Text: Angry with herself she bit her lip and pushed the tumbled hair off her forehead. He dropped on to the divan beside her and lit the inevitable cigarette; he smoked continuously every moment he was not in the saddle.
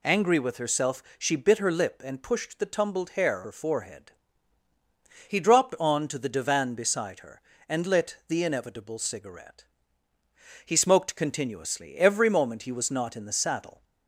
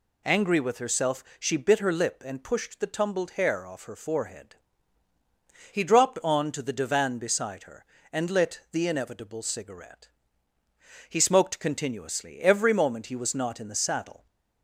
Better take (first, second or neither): second